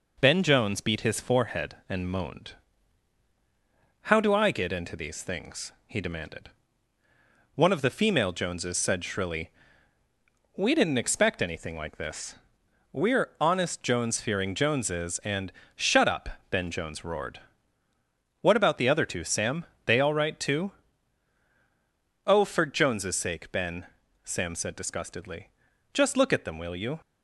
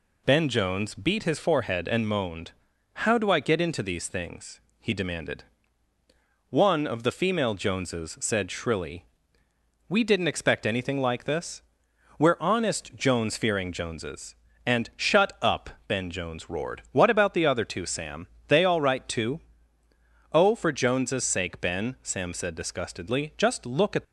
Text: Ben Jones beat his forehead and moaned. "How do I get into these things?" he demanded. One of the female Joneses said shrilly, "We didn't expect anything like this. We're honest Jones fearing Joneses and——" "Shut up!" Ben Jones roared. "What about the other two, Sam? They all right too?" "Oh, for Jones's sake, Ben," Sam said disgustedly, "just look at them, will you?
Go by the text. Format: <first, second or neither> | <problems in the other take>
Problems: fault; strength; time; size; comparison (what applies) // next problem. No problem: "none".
first | stops before "them will you"; at 24.0 s